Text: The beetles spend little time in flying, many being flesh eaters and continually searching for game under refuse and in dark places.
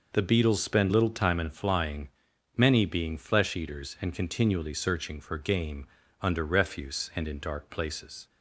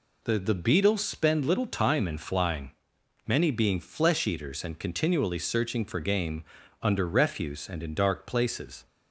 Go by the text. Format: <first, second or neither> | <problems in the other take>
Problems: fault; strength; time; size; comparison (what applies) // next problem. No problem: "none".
first | says "The" twice; at 0.3 s // pauses between "game" and "under"; at 6.4 s; 0.40 s long; slight in the first